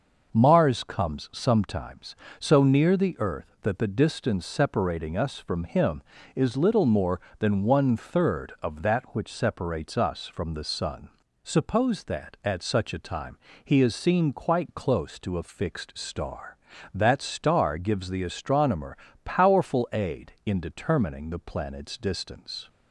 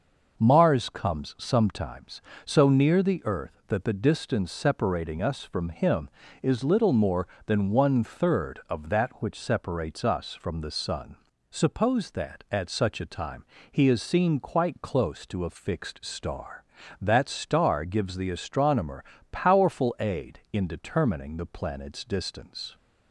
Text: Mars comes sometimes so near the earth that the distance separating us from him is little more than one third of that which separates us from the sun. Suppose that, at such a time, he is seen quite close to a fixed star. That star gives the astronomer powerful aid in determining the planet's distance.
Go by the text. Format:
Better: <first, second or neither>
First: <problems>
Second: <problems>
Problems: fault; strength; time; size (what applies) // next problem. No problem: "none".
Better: neither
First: pauses between "astronomer" and "powerful"; slight; at 18.9 s; 0.26 s long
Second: pauses between "astronomer" and "powerful"; slight; at 19.0 s; 0.26 s long